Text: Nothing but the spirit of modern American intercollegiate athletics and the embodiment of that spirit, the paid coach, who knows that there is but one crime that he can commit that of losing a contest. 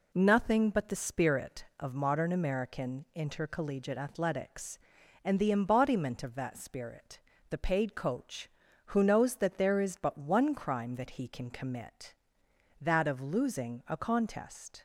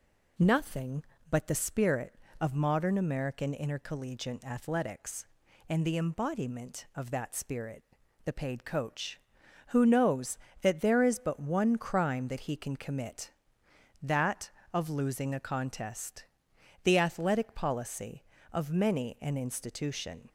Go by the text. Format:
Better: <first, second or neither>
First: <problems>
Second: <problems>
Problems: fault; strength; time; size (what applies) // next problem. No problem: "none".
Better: first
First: none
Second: goes on to say "The athletic policy of many an institution"; strong; from 16.8 s on; 3.4 s long